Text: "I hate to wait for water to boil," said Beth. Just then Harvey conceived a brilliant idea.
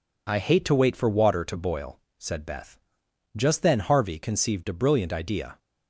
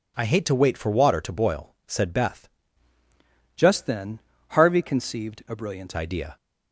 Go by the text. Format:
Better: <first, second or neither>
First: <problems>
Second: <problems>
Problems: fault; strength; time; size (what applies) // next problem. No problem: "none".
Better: first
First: none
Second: changes voice from "Just" to "brilliant"; from 3.5 to 5.9 s; 2.4 s long // pauses between "then" and "Harvey"; slight; at 4.2 s; 0.30 s long